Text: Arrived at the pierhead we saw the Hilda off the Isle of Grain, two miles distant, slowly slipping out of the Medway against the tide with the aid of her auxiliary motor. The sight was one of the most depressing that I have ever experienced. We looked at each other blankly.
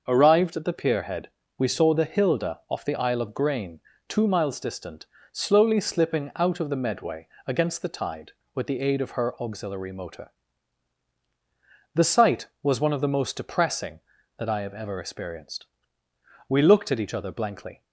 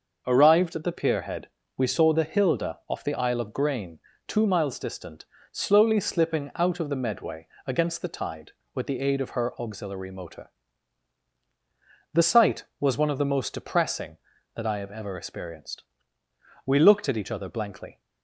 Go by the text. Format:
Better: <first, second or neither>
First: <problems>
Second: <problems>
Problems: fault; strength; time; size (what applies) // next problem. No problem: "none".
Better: neither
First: pauses between "pierhead" and "we"; slight; at 1.2 s; 0.28 s long // pauses between "Medway" and "against"; slight; at 7.2 s; 0.20 s long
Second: pauses between "pierhead" and "we"; slight; at 1.4 s; 0.28 s long // pauses between "Medway" and "against"; slight; at 7.4 s; 0.20 s long